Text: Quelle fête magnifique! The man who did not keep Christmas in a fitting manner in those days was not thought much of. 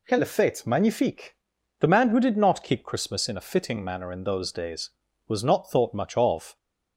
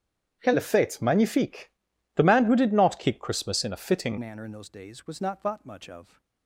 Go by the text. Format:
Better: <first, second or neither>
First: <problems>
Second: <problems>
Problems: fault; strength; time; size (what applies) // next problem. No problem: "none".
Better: first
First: none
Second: starts louder than the rest; strong; until 1.4 s; 9 dB // changes voice at "manner"; from 4.1 s on; 2.1 s long